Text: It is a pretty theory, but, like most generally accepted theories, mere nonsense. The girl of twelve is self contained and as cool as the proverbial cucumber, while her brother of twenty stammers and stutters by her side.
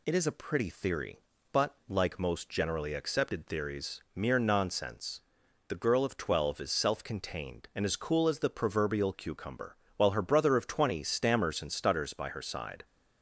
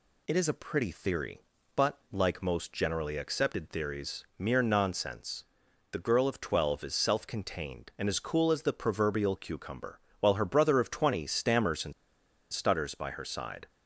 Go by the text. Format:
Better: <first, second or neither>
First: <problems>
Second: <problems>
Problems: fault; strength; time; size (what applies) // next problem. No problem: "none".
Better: first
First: none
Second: pauses between "and" and "stutters"; noticeable; at 11.9 s; 0.60 s long